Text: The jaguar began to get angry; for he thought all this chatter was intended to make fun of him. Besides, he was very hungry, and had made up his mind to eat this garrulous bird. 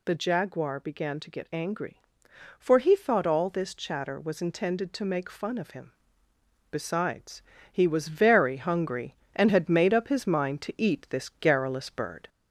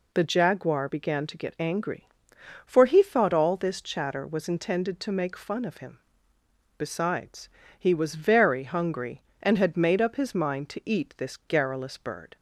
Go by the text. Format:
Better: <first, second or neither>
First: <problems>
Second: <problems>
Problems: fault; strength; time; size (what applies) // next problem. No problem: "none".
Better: second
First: gets louder; slight; throughout; 2.5 dB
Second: none